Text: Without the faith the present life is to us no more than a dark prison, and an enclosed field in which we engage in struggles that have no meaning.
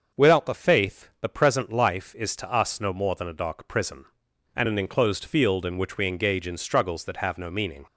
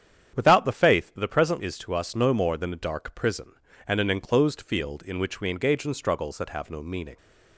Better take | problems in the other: first | starts louder than the rest; strong; until 1.3 s; 8.5 dB; also in the first // skips "life"; at 1.5 s

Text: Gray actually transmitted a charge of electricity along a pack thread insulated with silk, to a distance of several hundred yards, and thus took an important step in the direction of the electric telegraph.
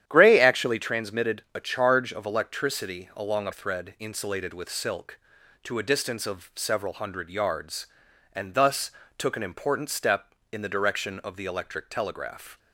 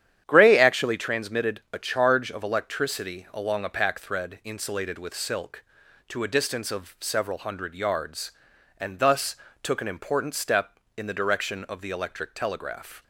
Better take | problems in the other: second | starts louder than the rest; strong; until 1.0 s; 10.5 dB; strong in the second // skips "pack"; at 3.5 s // pauses between "thus" and "took"; slight; at 8.8 s; 0.28 s long; slight in the second

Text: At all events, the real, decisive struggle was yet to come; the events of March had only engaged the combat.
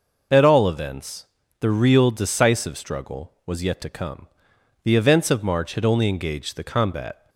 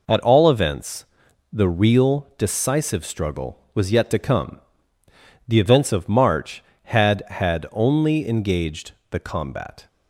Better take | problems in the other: first | says "had" twice; at 7.2 s // pauses between "engaged" and "the"; slight; at 8.9 s; 0.18 s long

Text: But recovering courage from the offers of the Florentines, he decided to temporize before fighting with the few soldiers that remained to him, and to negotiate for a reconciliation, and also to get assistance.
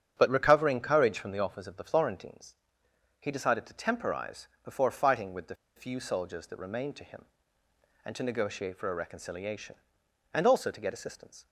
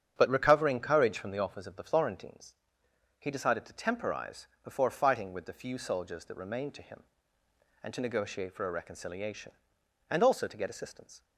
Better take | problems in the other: second | starts louder than the rest; strong; until 1.1 s; 8 dB; strong in the second // pauses between "temporize" and "before"; slight; at 4.4 s; 0.16 s long; slight in the second // pauses between "the" and "few"; slight; at 5.5 s; 0.22 s long

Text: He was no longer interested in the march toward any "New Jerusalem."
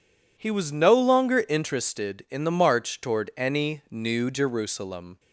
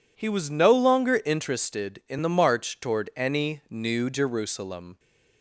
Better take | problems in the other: neither | none

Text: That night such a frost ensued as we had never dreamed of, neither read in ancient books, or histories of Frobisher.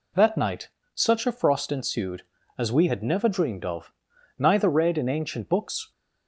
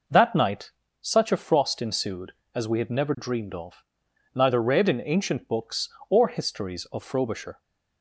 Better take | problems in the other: second | pauses between "night" and "such"; slight; at 0.6 s; 0.24 s long; slight in the second // stops before "or histories of Frobisher"; at 5.9 s

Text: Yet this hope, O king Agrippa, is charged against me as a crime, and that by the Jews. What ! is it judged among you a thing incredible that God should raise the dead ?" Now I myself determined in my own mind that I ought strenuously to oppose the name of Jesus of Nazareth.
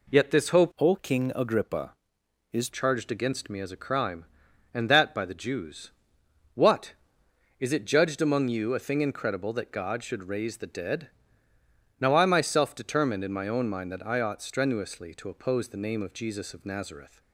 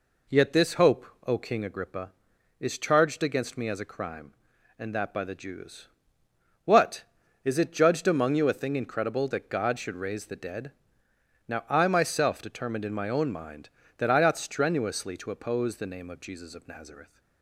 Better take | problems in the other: second | changes voice from "O" to "is"; from 0.7 to 2.6 s; 1.9 s long

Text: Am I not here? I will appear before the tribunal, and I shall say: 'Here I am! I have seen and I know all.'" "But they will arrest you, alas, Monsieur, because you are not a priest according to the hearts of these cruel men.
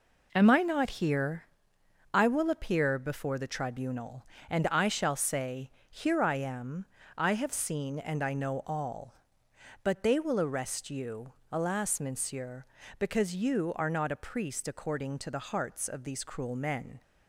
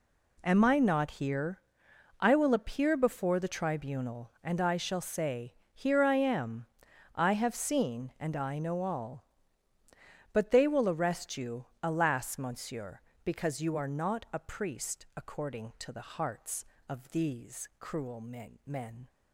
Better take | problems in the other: first | says "men" twice; at 18.6 s

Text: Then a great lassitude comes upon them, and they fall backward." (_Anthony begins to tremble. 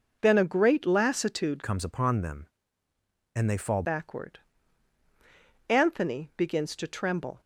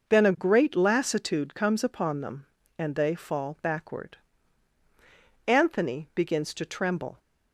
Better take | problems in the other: second | changes voice from "comes" to "fall"; from 1.6 to 3.8 s; 2.2 s long

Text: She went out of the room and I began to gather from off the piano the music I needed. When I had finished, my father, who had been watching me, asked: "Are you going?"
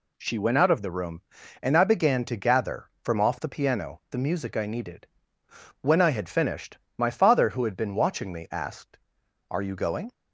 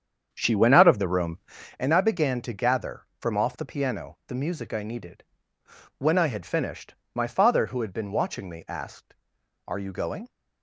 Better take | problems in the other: first | starts louder than the rest; strong; until 1.9 s; 8 dB

